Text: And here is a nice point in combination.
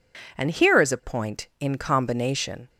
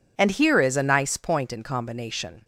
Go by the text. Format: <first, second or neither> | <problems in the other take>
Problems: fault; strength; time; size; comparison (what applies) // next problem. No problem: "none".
second | skips "nice"; at 1.0 s